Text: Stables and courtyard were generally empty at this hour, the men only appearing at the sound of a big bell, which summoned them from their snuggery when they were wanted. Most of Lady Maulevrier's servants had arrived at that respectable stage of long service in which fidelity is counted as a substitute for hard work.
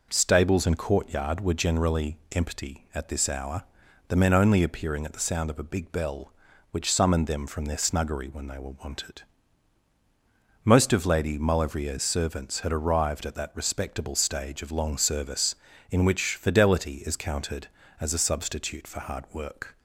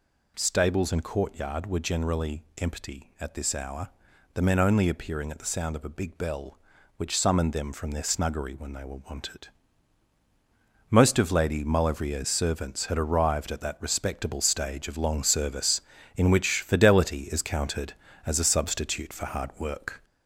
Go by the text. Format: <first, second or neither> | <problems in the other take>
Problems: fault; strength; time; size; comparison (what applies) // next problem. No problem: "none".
first | gets louder; noticeable; throughout; 4.5 dB // pauses between "generally" and "empty"; slight; at 2.4 s; 0.16 s long; slight in the first